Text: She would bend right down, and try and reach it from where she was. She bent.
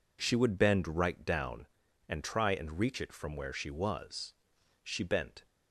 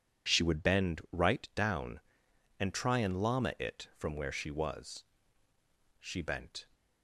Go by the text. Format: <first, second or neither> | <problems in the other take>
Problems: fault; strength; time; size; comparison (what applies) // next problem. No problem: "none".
first | says "llama" for "reach"; at 3.2 s